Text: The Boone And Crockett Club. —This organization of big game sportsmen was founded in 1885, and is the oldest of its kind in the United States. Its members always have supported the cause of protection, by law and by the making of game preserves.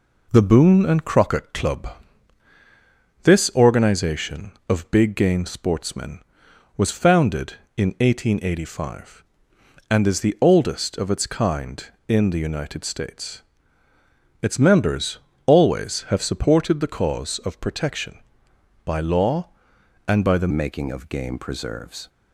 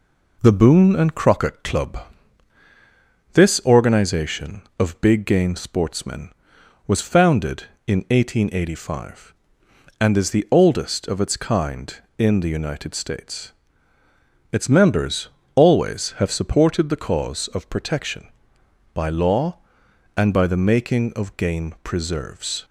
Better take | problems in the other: second | pauses between "members" and "always"; slight; at 15.1 s; 0.30 s long; slight in the second // changes voice at "making"; from 20.5 s on; 1.5 s long

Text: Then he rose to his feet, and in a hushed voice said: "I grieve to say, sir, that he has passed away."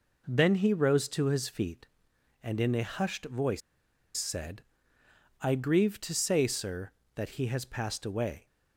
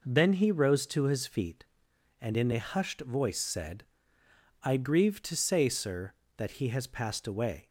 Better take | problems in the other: second | pauses between "voice" and "said"; noticeable; at 3.6 s; 0.57 s long

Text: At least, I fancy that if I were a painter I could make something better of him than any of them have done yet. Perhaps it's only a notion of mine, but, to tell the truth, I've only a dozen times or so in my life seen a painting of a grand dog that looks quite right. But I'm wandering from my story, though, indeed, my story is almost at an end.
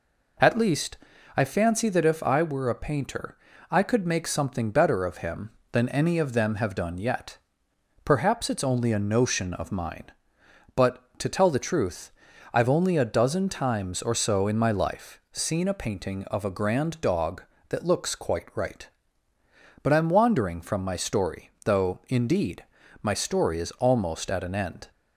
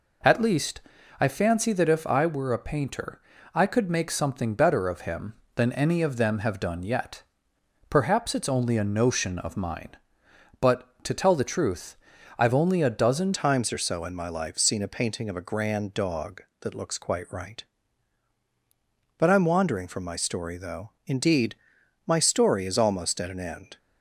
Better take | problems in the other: first | pauses between "painter" and "I"; slight; at 3.2 s; 0.32 s long; slight in the first // changes voice at "times"; from 13.3 s on; 10.4 s long

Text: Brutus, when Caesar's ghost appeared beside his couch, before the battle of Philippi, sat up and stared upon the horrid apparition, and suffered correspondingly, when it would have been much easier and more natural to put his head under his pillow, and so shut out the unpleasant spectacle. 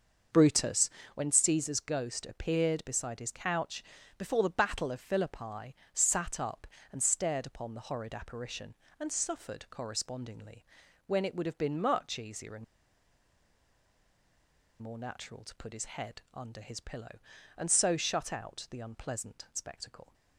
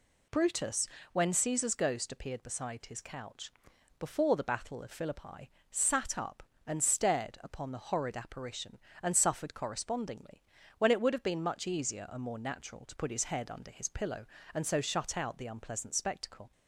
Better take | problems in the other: second | starts louder than the rest; until 1.5 s; 6.5 dB // pauses between "and" and "more"; strong; at 12.6 s; 2.1 s long

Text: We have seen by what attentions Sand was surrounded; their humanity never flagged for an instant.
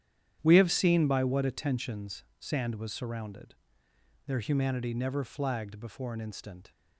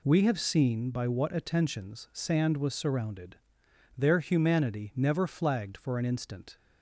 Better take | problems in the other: second | starts louder than the rest; strong; until 1.4 s; 10 dB // pauses between "attentions" and "Sand"; slight; at 2.2 s; 0.16 s long // says "before" for "for"; at 5.8 s

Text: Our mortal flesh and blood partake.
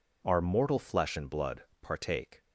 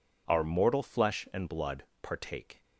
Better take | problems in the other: neither | pauses between "blood" and "partake"; slight; the same in both

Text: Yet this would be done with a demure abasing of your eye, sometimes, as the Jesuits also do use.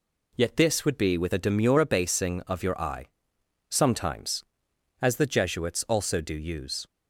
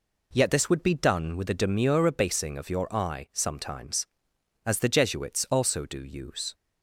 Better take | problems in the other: second | skips "done"; at 1.1 s

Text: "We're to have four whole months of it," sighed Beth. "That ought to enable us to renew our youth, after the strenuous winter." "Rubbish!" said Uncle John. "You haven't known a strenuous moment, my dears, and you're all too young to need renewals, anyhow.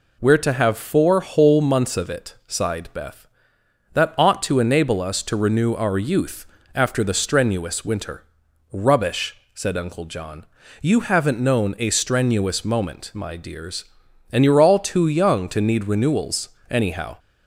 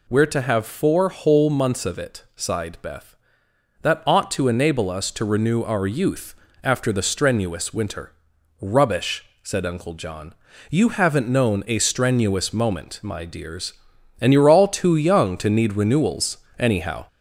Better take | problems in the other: first | gets louder; slight; throughout; 2.5 dB

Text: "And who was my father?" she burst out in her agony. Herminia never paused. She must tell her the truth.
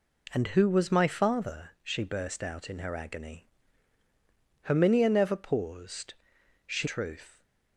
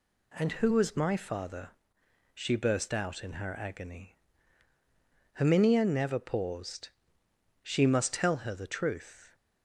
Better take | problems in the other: second | skips "must tell her the"; at 6.8 s

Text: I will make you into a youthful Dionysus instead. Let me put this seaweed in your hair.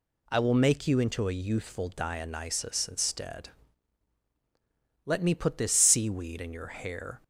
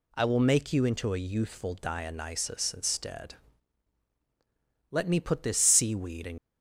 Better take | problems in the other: first | stops before "your hair"; at 6.3 s

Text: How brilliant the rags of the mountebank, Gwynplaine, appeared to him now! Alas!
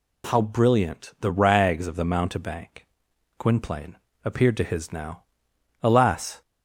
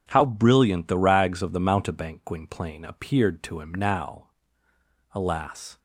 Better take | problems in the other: second | says "his" for "him"; at 4.6 s

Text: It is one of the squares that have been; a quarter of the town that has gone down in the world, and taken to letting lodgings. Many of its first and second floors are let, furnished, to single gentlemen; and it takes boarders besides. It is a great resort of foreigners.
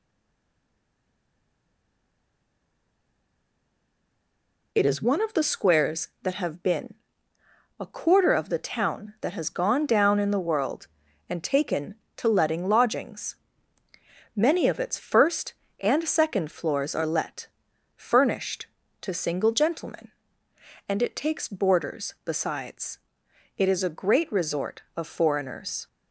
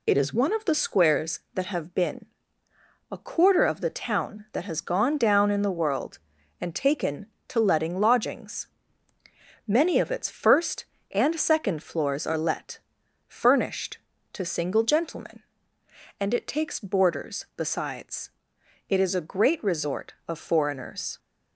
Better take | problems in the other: second | stays silent before the first word; strong; until 4.7 s; 4.7 s long

